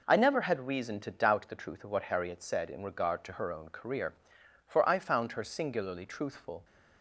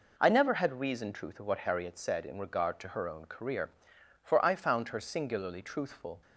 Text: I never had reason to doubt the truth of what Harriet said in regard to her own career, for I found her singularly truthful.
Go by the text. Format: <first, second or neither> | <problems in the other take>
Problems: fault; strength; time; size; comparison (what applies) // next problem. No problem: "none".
first | skips "to doubt the"; at 1.1 s